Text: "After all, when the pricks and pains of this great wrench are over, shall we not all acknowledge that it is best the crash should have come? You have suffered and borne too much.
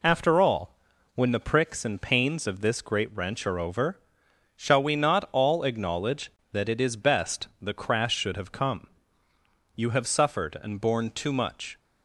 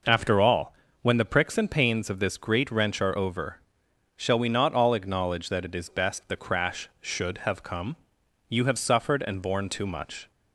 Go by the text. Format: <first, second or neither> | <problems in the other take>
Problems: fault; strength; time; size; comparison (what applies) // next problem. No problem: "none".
neither | none